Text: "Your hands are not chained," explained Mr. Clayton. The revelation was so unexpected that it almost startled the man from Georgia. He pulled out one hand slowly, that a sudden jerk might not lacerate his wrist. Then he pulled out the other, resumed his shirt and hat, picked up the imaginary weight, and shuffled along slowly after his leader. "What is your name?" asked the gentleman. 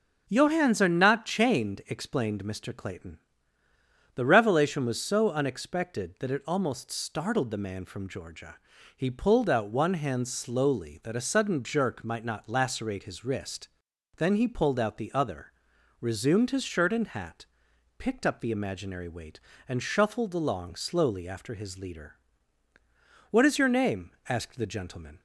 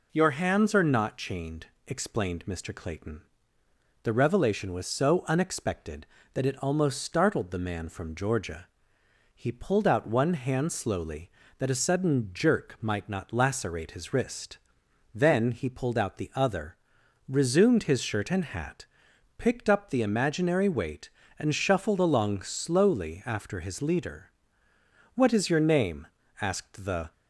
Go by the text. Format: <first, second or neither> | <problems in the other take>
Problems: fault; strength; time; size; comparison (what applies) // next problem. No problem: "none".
first | stops before "gentleman"; at 27.1 s